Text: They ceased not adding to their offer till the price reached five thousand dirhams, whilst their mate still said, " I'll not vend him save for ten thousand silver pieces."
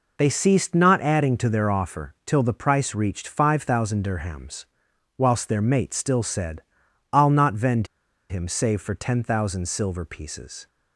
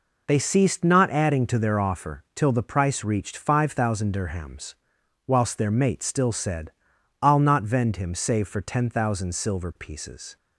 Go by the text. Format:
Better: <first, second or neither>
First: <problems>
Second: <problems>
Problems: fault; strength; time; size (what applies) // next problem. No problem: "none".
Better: second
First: pauses between "vend" and "him"; at 7.8 s; 0.44 s long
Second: none